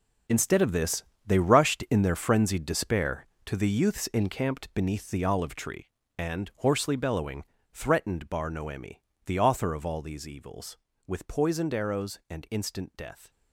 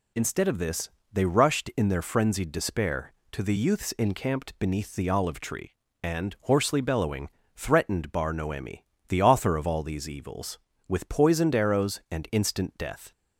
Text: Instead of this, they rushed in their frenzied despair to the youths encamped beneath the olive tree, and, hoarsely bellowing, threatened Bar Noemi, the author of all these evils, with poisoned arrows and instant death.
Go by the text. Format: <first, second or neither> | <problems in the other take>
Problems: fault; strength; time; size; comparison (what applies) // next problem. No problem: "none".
second | gets quieter; strong; throughout; 12 dB